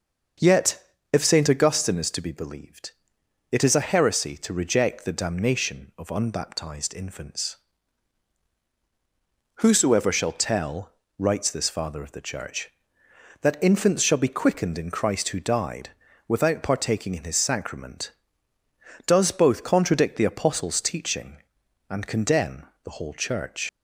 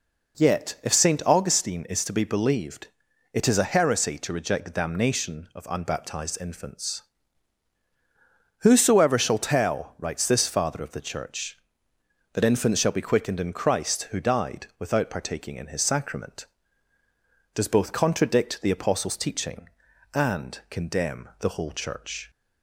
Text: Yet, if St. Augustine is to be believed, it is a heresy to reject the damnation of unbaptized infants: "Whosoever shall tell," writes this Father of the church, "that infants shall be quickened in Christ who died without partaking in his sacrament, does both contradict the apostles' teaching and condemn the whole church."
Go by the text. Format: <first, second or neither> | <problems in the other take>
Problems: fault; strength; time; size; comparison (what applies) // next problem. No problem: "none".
second | starts louder than the rest; until 1.6 s; 6.5 dB // pauses between "died" and "without"; at 15.9 s; 0.38 s long // pauses between "condemn" and "the"; slight; at 22.6 s; 0.20 s long // leaves "church" unfinished; at 23.6 s; 95 ms